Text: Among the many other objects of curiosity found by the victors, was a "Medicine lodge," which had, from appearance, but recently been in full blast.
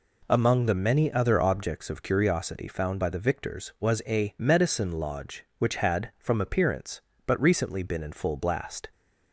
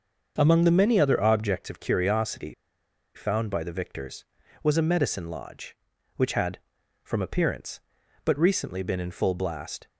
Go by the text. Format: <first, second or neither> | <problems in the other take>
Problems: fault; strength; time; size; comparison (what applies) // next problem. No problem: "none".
first | starts louder than the rest; noticeable; until 1.4 s; 6 dB // pauses between "curiosity" and "found"; noticeable; at 2.5 s; 0.62 s long